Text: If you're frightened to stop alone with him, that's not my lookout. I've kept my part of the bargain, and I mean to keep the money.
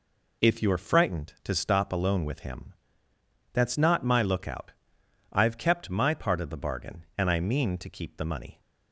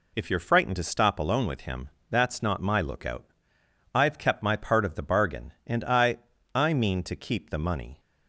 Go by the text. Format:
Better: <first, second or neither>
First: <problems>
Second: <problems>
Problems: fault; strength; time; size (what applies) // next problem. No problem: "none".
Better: first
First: none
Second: says "I" twice; at 6.5 s